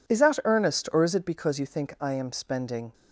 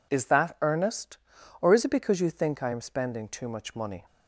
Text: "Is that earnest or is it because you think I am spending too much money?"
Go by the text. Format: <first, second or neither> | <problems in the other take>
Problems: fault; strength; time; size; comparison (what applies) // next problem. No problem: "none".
second | stops before "too much money"; at 2.9 s